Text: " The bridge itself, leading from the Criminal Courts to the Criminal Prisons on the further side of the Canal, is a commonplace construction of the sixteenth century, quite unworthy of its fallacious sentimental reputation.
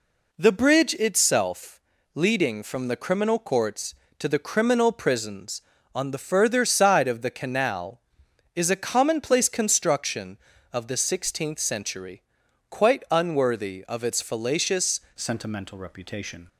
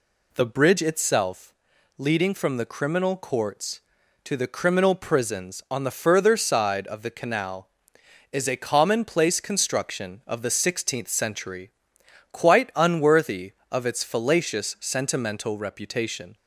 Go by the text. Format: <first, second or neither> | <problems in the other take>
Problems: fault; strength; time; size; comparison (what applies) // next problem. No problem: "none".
second | changes voice at "sentimental"; from 15.1 s on; 1.3 s long